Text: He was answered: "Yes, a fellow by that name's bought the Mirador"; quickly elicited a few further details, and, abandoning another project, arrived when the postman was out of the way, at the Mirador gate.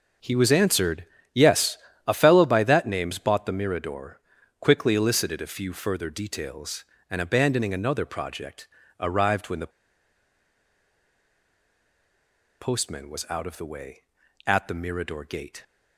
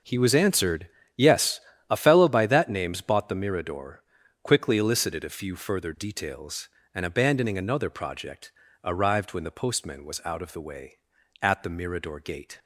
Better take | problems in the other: second | pauses between "the" and "postman"; strong; at 9.7 s; 2.9 s long

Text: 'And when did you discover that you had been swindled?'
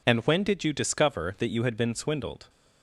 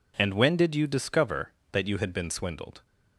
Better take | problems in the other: neither | none

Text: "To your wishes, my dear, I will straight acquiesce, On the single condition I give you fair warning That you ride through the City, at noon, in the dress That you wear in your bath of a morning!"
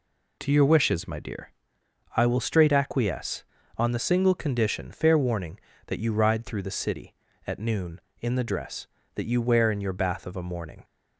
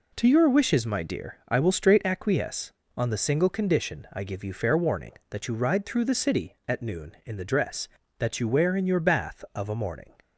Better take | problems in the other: second | skips "I give you"; at 4.9 s

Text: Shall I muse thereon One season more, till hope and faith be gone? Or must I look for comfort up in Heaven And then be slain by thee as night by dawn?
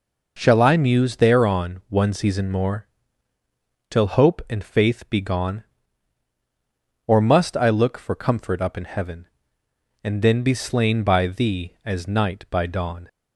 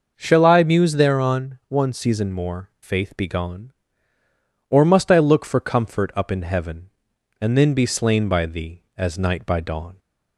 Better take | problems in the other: first | skips "till hope and"; at 2.7 s

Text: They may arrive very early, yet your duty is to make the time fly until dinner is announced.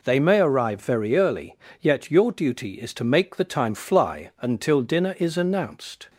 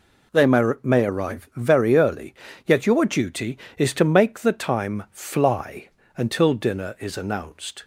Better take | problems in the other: first | says "may" twice; at 0.8 s // pauses between "fly" and "until"; slight; at 5.8 s; 0.30 s long

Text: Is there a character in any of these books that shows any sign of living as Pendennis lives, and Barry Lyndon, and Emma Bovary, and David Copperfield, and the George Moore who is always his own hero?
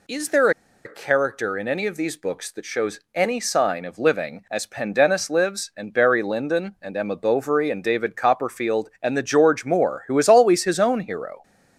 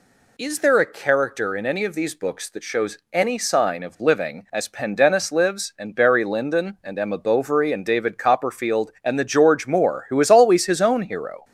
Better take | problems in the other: second | pauses between "there" and "a"; slight; at 0.5 s; 0.34 s long // pauses between "shows" and "any"; slight; at 2.9 s; 0.16 s long; slight in the second

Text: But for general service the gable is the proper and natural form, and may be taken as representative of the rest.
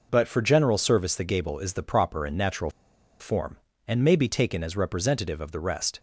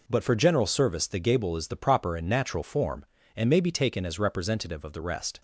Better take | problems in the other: second | pauses between "natural" and "form"; noticeable; at 2.7 s; 0.49 s long

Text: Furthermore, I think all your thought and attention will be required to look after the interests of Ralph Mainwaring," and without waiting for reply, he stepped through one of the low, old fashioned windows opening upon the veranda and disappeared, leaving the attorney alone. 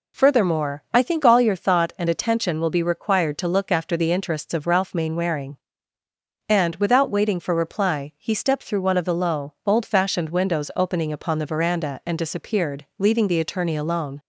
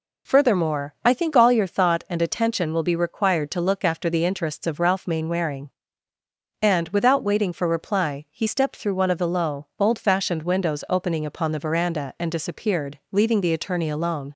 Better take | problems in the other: neither | none

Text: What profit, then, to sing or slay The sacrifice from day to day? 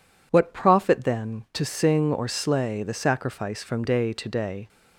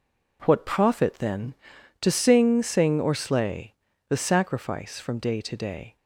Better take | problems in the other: first | says "sing" twice; at 2.6 s // pauses between "slay" and "The"; slight; at 3.7 s; 0.34 s long

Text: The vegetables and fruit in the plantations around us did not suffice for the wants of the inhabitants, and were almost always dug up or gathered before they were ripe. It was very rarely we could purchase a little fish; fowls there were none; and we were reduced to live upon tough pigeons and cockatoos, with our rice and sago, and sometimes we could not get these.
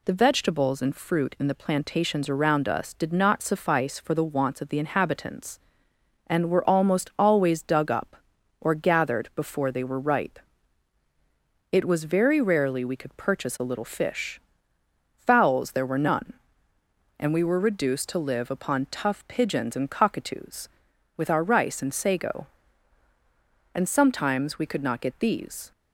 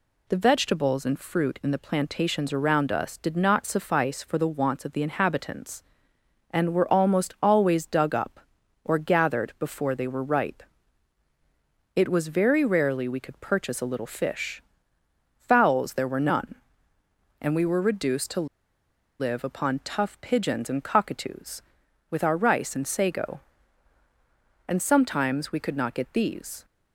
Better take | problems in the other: first | pauses between "to" and "live"; noticeable; at 18.4 s; 0.72 s long

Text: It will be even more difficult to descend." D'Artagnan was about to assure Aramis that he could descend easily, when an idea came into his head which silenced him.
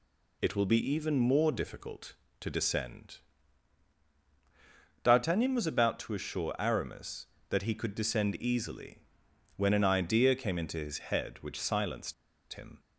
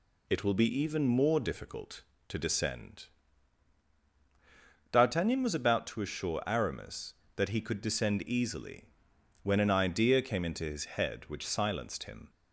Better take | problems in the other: second | pauses between "silenced" and "him"; at 12.1 s; 0.39 s long

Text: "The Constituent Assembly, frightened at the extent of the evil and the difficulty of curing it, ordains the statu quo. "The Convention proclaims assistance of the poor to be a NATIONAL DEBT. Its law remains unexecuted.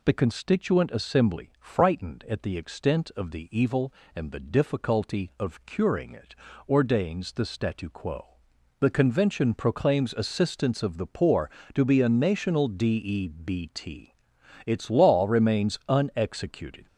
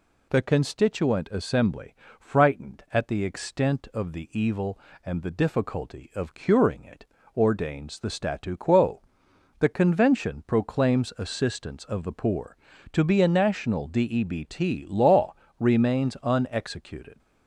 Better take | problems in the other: first | skips "Its"; at 14.8 s // pauses between "law" and "remains"; slight; at 15.3 s; 0.24 s long

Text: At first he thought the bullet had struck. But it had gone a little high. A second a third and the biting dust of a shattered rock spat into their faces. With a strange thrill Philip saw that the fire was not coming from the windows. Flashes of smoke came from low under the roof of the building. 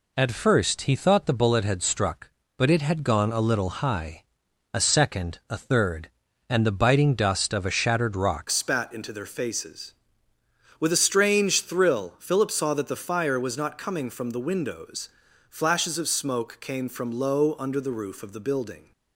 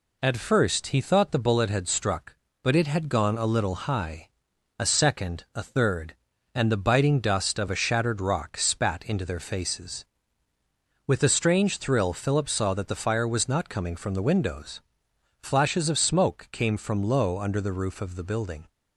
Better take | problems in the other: second | changes voice at "spat"; from 8.4 s on; 10.5 s long

